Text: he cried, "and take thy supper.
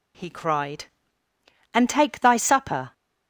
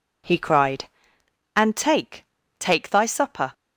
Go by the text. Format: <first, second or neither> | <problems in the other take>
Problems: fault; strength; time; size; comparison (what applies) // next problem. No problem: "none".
first | says "take" twice; at 2.5 s